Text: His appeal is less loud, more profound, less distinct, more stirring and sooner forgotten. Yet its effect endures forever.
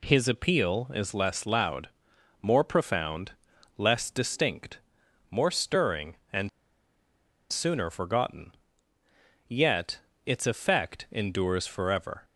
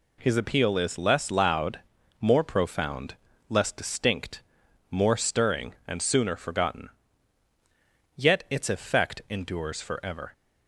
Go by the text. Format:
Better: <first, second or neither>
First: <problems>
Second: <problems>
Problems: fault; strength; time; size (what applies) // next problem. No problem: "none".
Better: second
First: pauses between "and" and "sooner"; at 6.4 s; 1.0 s long // pauses between "Yet" and "its"; slight; at 9.9 s; 0.28 s long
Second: none